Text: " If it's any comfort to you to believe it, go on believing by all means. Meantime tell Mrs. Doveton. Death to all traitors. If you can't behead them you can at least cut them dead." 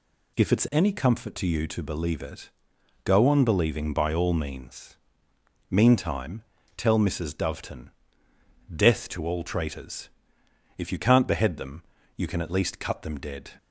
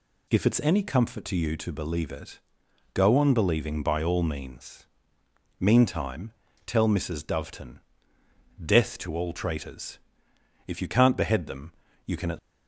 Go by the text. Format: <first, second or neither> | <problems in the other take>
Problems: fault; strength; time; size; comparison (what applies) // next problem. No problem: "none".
first | pauses between "Meantime" and "tell"; slight; at 6.3 s; 0.32 s long; slight in the first // pauses between "them" and "you"; slight; at 11.7 s; 0.32 s long; slight in the first // stops before "least cut them dead"; at 12.3 s